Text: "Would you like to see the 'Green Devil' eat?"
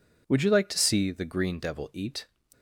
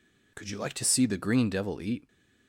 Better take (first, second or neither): first